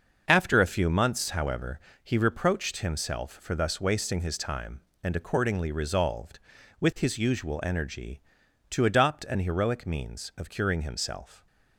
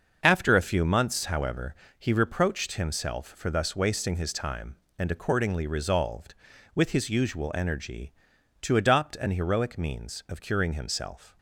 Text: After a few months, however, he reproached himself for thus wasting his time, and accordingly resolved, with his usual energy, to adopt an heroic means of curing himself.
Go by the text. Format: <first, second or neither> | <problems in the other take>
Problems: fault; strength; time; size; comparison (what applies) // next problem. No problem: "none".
neither | starts louder than the rest; the same in both